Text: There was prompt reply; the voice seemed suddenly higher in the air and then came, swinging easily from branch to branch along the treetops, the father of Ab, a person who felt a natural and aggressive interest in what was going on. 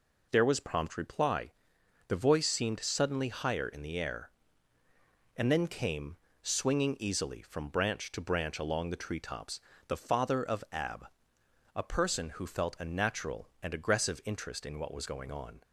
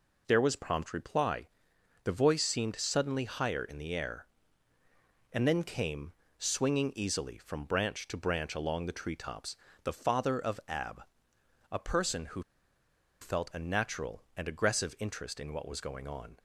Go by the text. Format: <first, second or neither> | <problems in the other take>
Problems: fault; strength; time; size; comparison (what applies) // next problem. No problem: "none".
first | pauses between "who" and "felt"; noticeable; at 12.4 s; 0.80 s long